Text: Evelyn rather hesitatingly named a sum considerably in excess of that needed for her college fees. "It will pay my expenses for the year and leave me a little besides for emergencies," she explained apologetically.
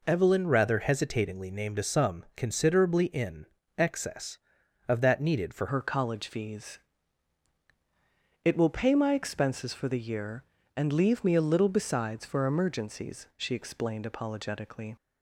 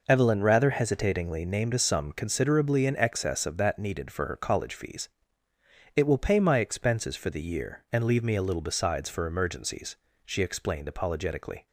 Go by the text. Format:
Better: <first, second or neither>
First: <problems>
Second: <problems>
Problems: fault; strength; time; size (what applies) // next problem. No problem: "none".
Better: second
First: pauses between "in" and "excess"; slight; at 3.4 s; 0.32 s long // changes voice at "her"; from 5.6 s on; 9.3 s long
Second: none